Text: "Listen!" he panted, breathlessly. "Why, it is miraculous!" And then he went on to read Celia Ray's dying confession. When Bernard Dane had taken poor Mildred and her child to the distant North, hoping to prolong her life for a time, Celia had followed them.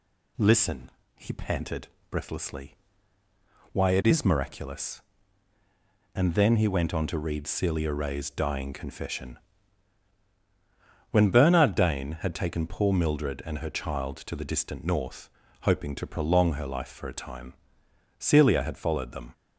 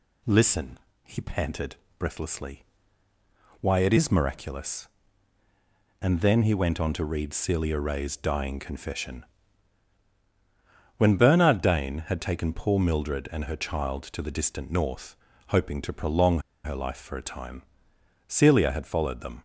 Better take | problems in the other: first | pauses between "prolong" and "her"; slight; at 16.3 s; 0.25 s long

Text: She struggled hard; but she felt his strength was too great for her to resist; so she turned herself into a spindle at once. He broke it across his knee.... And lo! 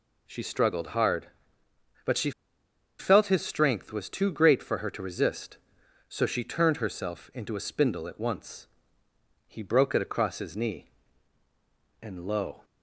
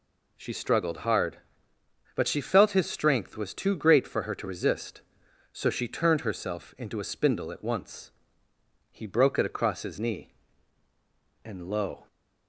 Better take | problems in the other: second | pauses between "she" and "felt"; noticeable; at 2.3 s; 0.68 s long

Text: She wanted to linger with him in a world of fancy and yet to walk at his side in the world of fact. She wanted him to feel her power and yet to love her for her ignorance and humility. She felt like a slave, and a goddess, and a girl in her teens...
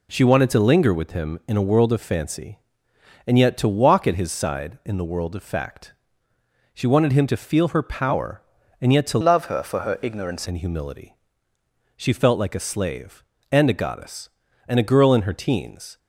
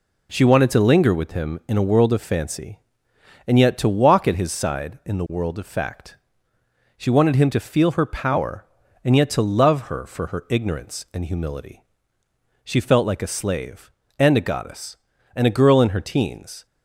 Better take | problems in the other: second | changes voice from "love" to "ignorance"; from 9.2 to 10.4 s; 1.2 s long

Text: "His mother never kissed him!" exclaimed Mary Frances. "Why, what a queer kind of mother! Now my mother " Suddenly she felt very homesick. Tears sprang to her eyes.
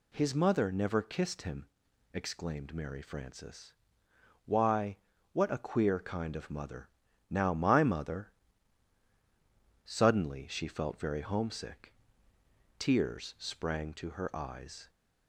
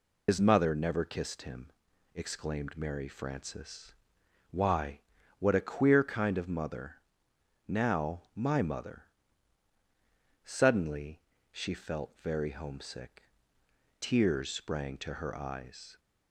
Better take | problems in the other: first | loses the start of "His"; at 0.2 s; 95 ms // pauses between "Suddenly" and "she"; slight; at 11.1 s; 0.32 s long

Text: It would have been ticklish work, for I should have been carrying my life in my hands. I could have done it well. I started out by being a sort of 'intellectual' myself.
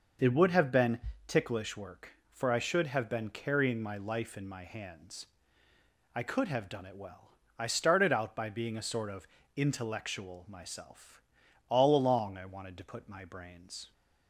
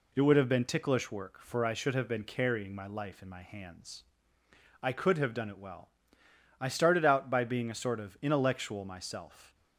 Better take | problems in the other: second | pauses between "been" and "ticklish"; slight; at 0.9 s; 0.30 s long // pauses between "of" and "intellectual"; slight; at 9.2 s; 0.30 s long // goes on to say "All along I wanted to put my brains"; strong; from 11.6 s on; 2.2 s long

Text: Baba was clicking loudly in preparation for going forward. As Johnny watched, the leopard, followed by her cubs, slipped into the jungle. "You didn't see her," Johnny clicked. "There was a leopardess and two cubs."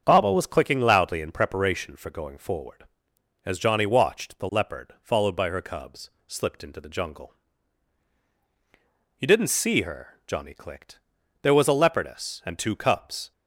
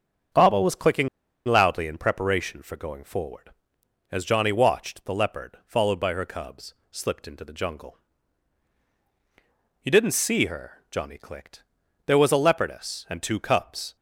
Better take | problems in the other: first | starts louder than the rest; strong; until 1.7 s; 7.5 dB; strong in the first // pauses between "clicking" and "loudly"; at 1.0 s; 0.39 s long

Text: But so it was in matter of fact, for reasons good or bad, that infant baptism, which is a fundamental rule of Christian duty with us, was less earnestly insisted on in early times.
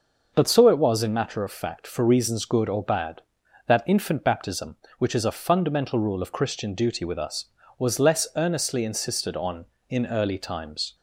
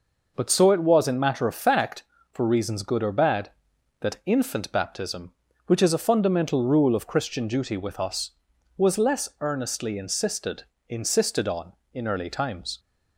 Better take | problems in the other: first | says "insisted" twice; at 10.8 s

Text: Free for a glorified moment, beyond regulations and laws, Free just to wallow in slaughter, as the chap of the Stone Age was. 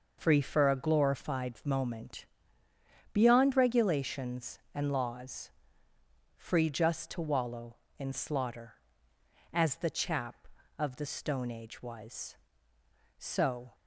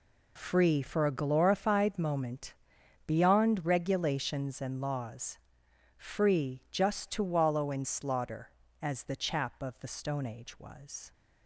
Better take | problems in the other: second | goes on to say "So"; from 13.1 s on; 0.58 s long

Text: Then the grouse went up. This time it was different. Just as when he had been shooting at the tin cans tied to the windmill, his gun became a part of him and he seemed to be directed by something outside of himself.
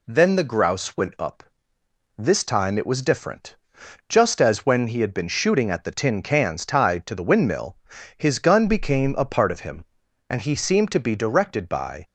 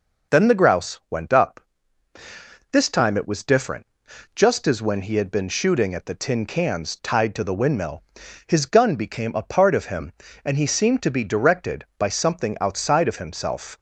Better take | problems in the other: second | stops before "something outside of himself"; at 12.0 s

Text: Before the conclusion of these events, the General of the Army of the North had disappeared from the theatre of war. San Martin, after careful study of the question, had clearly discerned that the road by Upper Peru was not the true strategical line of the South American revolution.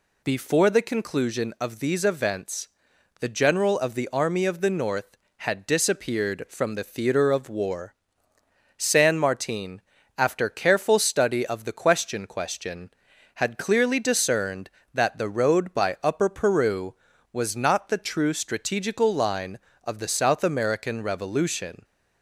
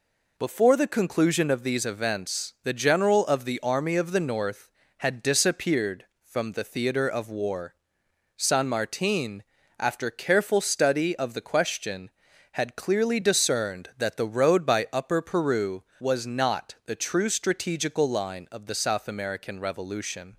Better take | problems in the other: second | says "question" twice; at 12.2 s

